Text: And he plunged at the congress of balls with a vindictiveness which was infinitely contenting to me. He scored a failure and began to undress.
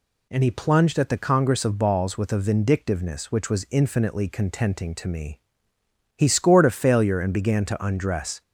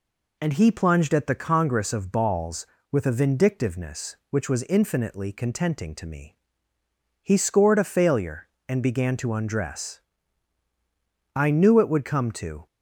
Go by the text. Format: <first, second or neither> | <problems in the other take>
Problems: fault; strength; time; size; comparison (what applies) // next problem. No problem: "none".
first | goes on to say "I knew it would come to"; from 11.3 s on; 1.3 s long